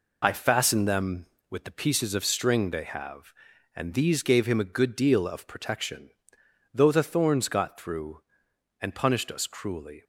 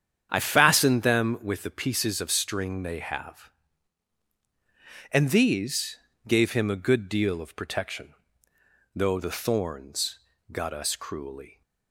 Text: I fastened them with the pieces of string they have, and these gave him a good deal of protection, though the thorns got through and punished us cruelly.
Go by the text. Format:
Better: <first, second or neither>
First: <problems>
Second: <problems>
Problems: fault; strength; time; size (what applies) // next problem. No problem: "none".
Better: first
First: none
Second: starts louder than the rest; strong; until 1.3 s; 8.5 dB // pauses between "these" and "gave"; slight; at 5.9 s; 0.30 s long // pauses between "thorns" and "got"; slight; at 10.1 s; 0.32 s long // skips "through and punished"; at 10.7 s